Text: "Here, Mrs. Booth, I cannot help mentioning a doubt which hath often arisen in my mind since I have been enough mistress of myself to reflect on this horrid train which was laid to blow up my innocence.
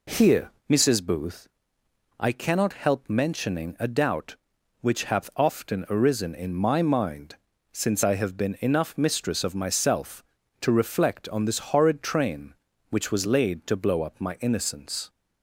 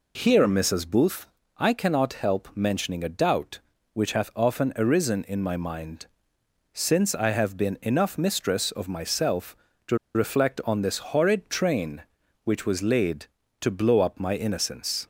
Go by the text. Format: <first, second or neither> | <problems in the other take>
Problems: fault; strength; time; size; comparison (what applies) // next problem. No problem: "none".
first | pauses between "mind" and "since"; noticeable; at 6.0 s; 0.66 s long; also in the first // pauses between "to" and "reflect"; slight; at 9.9 s; 0.17 s long // pauses between "this" and "horrid"; slight; at 10.9 s; 0.16 s long